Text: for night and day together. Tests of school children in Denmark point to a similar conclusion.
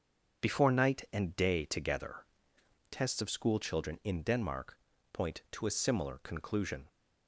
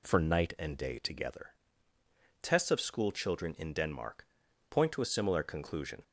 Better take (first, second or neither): second